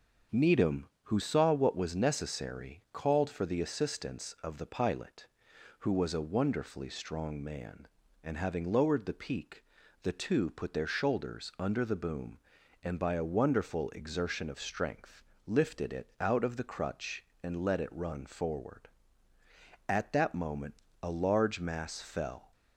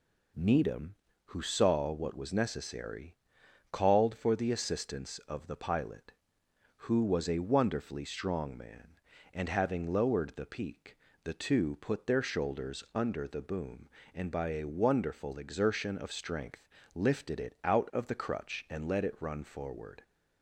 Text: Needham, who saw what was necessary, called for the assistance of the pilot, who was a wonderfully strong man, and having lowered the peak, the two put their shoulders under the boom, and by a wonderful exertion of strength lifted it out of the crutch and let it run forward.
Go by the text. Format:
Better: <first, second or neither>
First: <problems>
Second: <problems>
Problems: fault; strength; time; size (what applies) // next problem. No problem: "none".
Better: second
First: starts louder than the rest; noticeable; until 1.4 s; 6 dB // pauses between "strength" and "lifted"; slight; at 15.2 s; 0.24 s long // goes on to say "At that moment a large mass fell"; strong; from 19.8 s on; 2.6 s long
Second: pauses between "strength" and "lifted"; slight; at 16.6 s; 0.28 s long